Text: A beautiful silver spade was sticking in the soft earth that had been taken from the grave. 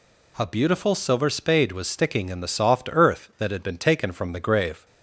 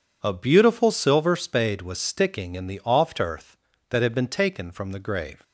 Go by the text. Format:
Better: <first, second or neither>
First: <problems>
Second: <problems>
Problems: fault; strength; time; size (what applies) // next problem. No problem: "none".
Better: first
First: none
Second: says "oft" for "soft"; at 2.8 s